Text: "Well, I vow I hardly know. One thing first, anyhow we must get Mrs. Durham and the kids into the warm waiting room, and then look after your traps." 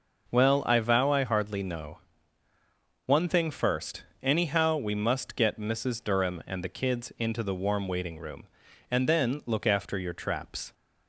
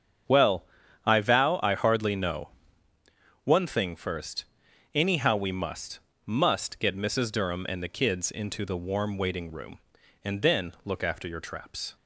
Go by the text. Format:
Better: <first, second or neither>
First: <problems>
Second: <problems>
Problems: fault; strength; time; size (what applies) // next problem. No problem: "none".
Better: first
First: none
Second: starts louder than the rest; strong; until 1.7 s; 8 dB // says "must" twice; at 6.2 s